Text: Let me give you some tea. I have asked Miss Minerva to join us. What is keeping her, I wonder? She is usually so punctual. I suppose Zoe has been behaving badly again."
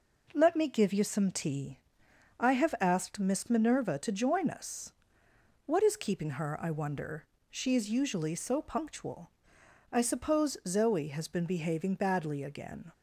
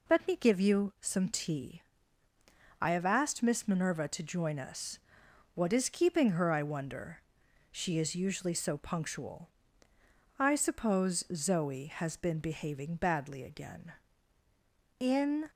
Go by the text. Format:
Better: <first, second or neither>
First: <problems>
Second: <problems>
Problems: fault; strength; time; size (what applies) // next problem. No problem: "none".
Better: first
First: none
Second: goes on to say "In"; slight; from 14.9 s on; 0.48 s long